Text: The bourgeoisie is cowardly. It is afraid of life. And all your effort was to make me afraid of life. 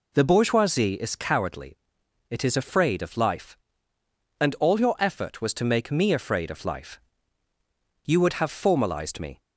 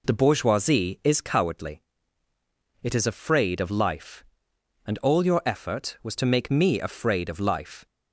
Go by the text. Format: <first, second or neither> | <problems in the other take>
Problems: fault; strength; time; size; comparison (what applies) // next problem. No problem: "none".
second | goes on to say "You would have formalized me"; from 8.0 s on; 1.3 s long